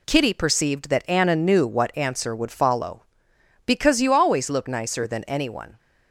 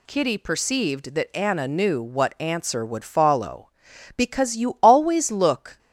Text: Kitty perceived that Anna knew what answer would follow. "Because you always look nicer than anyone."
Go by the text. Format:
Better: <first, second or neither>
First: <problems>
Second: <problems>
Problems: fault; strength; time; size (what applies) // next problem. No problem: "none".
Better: first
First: none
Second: stops before "nicer than anyone"; at 5.7 s